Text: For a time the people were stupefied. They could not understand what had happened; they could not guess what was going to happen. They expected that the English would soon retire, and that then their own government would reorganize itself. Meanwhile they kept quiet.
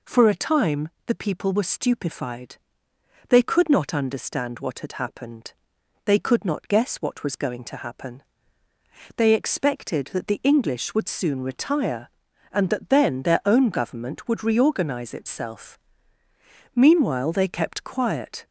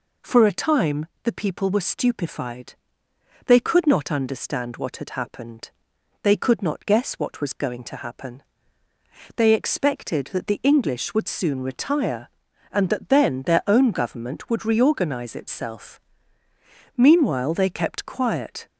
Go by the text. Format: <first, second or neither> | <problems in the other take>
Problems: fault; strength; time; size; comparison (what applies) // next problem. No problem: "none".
neither | pauses between "time" and "the"; slight; the same in both